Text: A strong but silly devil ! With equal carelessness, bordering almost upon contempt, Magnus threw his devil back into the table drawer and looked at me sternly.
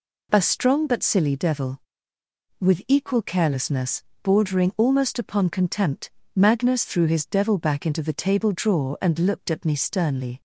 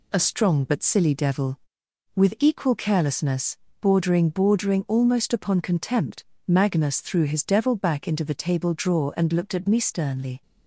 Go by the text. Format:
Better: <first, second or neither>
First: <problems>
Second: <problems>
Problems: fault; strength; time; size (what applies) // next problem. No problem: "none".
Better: first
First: none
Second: says "bordering" twice; at 4.2 s